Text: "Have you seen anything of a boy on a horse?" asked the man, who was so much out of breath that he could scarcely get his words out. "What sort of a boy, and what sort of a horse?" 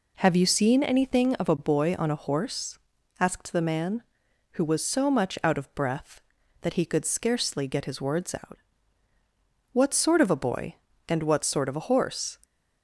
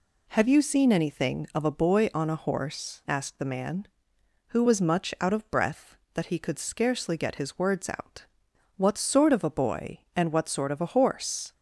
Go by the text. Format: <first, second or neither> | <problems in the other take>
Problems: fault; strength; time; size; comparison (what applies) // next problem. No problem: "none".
first | skips "so"; at 4.8 s